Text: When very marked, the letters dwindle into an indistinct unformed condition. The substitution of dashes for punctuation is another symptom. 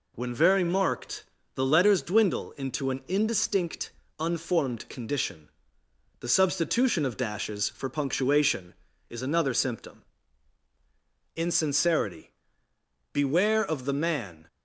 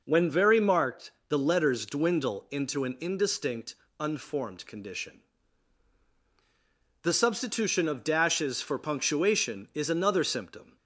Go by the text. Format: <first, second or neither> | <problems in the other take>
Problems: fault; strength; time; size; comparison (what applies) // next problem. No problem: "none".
second | pauses between "indistinct" and "unformed"; slight; at 3.9 s; 0.26 s long; slight in the second // goes on to say "Insincerity Beware of the man"; strong; from 11.3 s on; 3.1 s long